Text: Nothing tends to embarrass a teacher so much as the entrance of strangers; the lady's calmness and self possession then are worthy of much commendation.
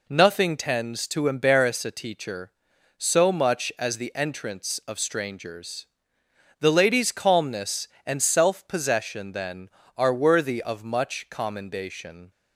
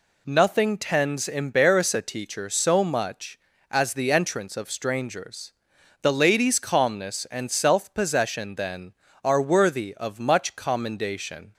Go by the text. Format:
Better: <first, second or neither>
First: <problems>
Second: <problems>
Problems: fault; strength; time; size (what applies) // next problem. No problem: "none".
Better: first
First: none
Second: skips "to"; at 1.2 s